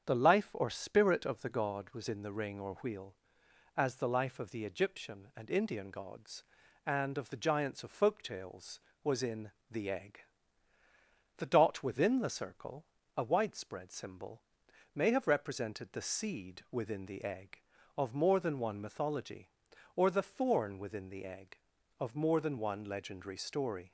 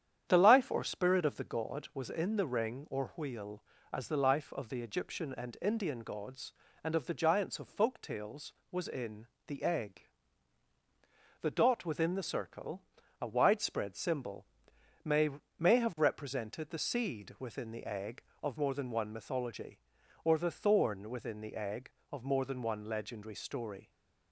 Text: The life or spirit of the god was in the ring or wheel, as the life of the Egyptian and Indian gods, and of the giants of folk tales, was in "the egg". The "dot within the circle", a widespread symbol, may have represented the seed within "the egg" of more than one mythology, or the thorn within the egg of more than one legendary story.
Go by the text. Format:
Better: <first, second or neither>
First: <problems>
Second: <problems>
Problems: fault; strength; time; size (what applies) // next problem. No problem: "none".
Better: first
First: starts louder than the rest; strong; until 1.1 s; 8 dB // pauses between "in" and "the"; slight; at 9.5 s; 0.18 s long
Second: starts louder than the rest; strong; until 1.2 s; 9.5 dB // pauses between "in" and "the"; slight; at 9.2 s; 0.20 s long // says "may" twice; at 15.5 s